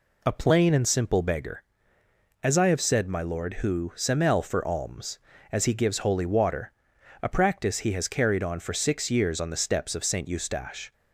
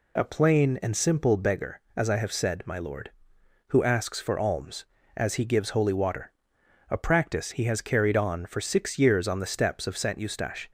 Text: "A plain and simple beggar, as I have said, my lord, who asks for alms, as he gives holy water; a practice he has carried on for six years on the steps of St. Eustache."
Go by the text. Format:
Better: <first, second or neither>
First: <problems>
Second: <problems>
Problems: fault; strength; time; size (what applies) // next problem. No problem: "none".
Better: second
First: says "semel" for "asks"; at 3.9 s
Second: none